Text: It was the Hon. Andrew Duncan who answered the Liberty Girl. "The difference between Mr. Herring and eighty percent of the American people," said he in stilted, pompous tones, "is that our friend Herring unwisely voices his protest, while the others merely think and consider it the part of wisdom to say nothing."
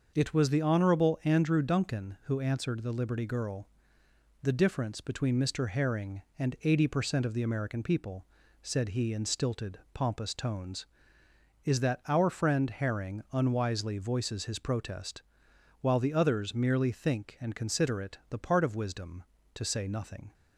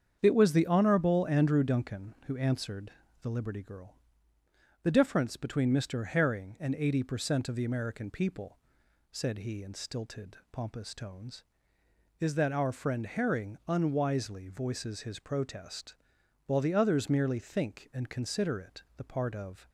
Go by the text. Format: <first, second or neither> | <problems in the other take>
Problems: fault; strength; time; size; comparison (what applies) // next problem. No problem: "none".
first | starts louder than the rest; strong; until 1.2 s; 7.5 dB; also in the first // pauses between "answered" and "the"; slight; at 2.9 s; 0.30 s long // stops before "wisdom to say nothing"; at 19.6 s